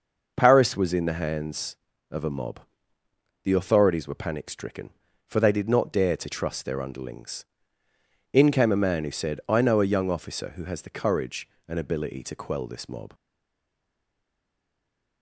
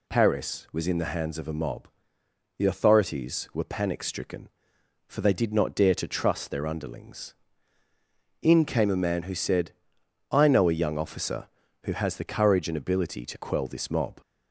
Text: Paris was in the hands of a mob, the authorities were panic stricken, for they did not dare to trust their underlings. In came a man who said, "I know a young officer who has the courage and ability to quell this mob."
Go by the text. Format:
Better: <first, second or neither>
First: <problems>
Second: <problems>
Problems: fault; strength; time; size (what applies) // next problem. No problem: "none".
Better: second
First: stays silent after the last word; noticeable; from 13.1 s on; 2.1 s long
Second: none